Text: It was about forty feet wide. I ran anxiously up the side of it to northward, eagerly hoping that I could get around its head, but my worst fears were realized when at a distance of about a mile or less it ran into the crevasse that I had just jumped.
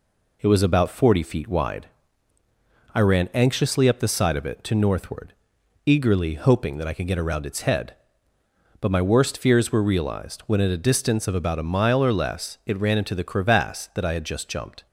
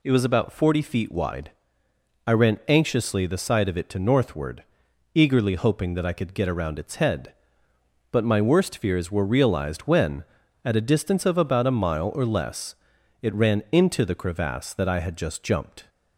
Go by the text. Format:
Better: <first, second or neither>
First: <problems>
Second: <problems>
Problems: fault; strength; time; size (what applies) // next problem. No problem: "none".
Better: first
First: none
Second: skips "up"; at 3.2 s // pauses between "less" and "it"; noticeable; at 12.7 s; 0.48 s long